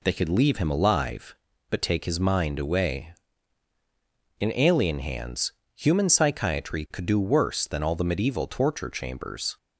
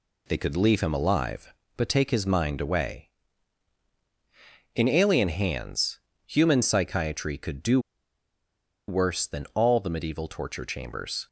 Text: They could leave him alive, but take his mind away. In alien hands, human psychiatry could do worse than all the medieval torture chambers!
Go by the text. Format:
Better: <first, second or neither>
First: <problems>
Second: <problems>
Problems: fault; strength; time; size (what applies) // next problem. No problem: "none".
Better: first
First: none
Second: pauses between "do" and "worse"; at 7.7 s; 1.0 s long